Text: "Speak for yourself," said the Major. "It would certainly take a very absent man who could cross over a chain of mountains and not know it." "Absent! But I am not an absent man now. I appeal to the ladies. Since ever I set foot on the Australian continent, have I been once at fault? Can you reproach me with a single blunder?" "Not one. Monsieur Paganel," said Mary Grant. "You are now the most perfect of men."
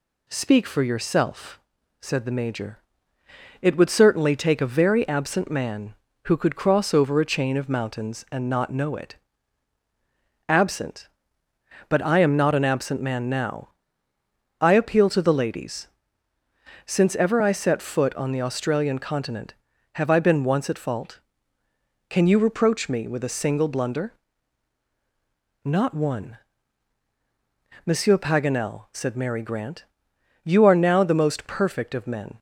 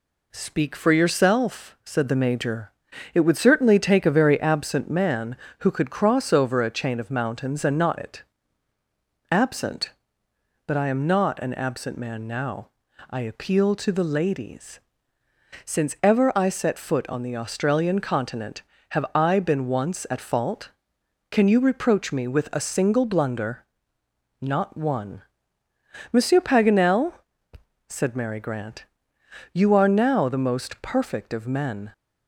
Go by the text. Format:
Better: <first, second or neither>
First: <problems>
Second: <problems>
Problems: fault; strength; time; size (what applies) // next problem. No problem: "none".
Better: first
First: none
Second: skips "know"; at 7.9 s